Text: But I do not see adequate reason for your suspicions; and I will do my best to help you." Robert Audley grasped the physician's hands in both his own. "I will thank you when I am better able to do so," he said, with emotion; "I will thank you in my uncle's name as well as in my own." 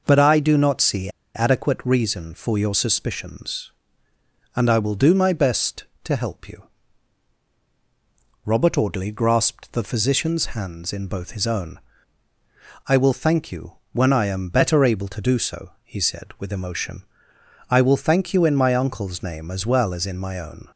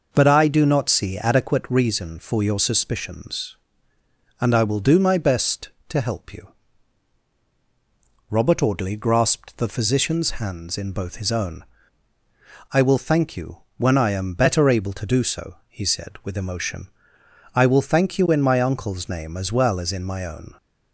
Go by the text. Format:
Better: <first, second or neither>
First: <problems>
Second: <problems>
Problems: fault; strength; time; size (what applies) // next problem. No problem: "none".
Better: second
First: pauses between "see" and "adequate"; slight; at 1.0 s; 0.25 s long // pauses between "you" and "when"; slight; at 13.7 s; 0.18 s long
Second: pauses between "you" and "when"; slight; at 13.5 s; 0.18 s long